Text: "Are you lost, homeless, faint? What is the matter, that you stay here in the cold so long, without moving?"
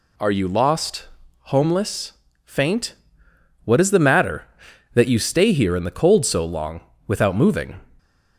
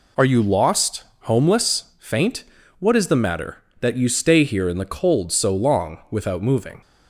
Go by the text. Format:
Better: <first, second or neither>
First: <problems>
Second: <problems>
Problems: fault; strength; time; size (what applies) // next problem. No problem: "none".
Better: neither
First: none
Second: none